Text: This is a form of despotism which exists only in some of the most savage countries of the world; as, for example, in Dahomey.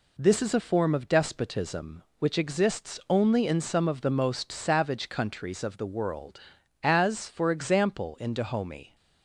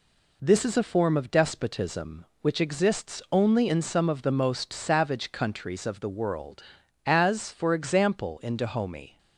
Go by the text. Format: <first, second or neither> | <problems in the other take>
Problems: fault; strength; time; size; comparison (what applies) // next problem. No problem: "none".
neither | none